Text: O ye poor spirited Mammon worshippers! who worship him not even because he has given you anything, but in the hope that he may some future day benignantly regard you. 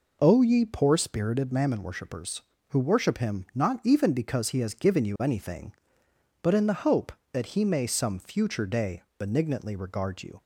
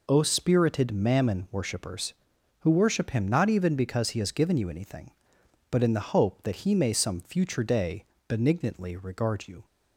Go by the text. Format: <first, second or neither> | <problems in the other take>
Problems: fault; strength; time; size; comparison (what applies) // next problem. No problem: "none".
first | skips "ye poor"; at 0.2 s // pauses between "day" and "benignantly"; slight; at 8.0 s; 0.22 s long